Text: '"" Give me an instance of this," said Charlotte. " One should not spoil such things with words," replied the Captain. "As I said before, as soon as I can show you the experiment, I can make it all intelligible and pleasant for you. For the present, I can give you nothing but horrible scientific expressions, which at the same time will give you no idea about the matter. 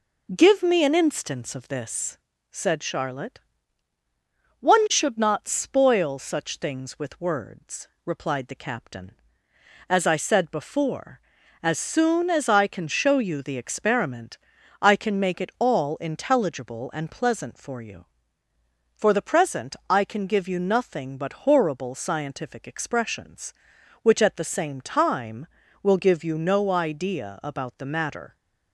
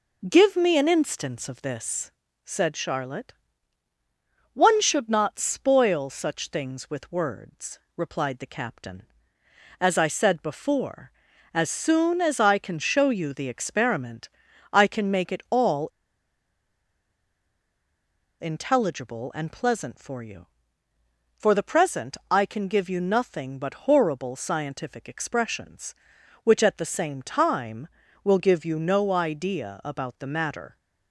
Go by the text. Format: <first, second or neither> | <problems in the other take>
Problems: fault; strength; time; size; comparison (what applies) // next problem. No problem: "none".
first | pauses between "all" and "intelligible"; strong; at 15.8 s; 2.5 s long